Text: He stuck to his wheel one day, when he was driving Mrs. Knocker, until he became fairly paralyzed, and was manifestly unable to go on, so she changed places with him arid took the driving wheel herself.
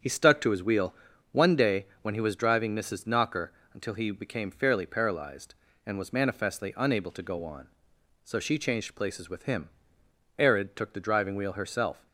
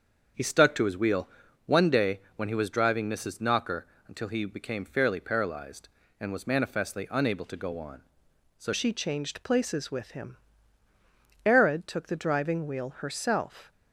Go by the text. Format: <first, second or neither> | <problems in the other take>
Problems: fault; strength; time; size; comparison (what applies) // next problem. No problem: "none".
first | starts louder than the rest; until 1.7 s; 7 dB; strong in the first // pauses between "wheel" and "one"; at 1.2 s; 0.38 s long; also in the first // changes voice at "she"; from 8.7 s on; 5.0 s long // pauses between "him" and "arid"; at 10.3 s; 1.1 s long; noticeable in the first